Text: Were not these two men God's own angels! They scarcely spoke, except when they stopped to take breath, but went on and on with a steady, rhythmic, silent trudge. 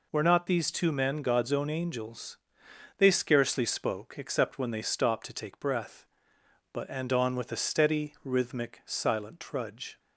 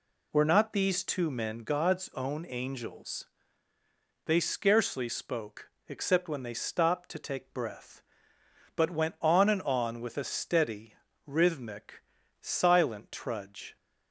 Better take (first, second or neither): second